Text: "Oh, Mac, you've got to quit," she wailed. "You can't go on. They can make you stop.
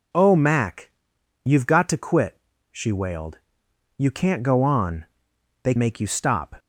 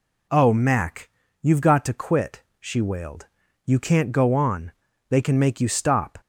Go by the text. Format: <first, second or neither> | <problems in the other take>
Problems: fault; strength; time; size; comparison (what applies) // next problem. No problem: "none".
second | skips "can"; at 5.7 s